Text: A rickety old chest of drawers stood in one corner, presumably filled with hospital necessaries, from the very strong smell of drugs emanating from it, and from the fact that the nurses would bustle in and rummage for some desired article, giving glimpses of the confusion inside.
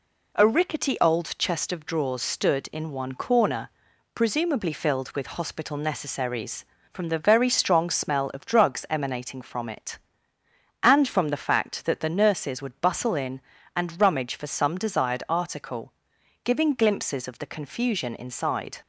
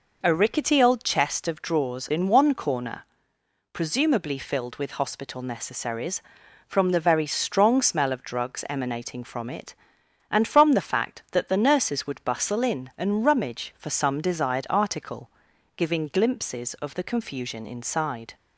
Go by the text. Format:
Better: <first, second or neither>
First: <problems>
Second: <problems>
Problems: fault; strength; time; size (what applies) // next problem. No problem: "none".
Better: first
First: none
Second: skips "stood"; at 2.1 s